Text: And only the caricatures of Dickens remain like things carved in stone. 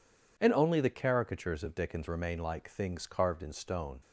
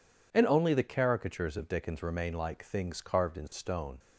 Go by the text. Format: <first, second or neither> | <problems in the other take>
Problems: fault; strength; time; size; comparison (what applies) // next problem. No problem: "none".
neither | none